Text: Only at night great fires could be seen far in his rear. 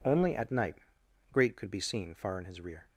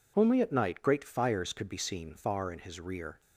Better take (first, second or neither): second